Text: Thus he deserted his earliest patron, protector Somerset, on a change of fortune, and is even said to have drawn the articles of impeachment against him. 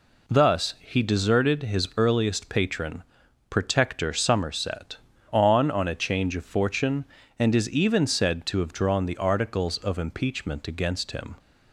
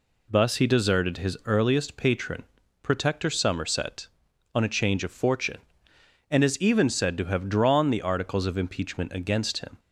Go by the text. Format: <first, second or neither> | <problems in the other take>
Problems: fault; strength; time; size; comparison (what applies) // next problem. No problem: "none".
second | says "on" twice; at 5.7 s